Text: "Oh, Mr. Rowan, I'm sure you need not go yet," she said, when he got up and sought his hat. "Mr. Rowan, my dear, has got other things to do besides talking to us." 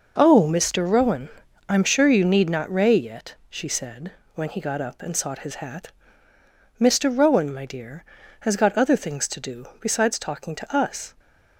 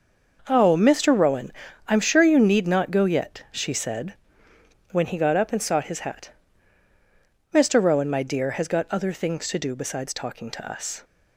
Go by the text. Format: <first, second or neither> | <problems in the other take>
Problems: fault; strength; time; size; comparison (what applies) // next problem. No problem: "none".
second | says "ray" for "go"; at 2.7 s